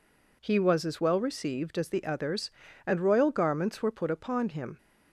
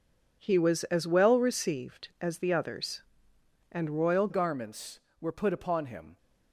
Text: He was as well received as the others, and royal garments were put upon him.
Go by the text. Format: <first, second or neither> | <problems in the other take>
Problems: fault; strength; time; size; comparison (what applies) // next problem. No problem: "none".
first | changes voice at "garments"; from 4.2 s on; 1.9 s long